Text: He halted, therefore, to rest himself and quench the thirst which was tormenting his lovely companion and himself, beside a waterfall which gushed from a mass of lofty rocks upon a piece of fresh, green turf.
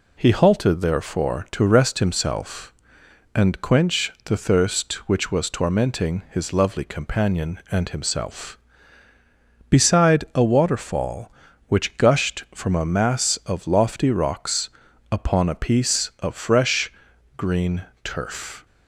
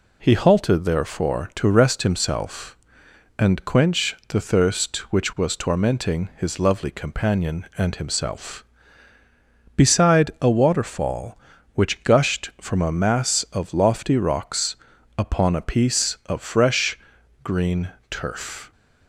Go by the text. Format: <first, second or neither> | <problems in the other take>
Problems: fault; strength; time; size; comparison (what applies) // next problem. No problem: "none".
neither | pauses between "rocks" and "upon"; the same in both // pauses between "green" and "turf"; slight; the same in both